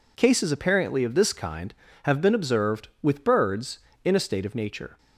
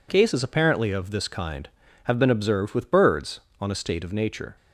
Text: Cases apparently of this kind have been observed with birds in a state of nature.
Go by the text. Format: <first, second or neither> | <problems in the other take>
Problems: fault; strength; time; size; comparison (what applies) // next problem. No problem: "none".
first | says "on" for "in"; at 3.6 s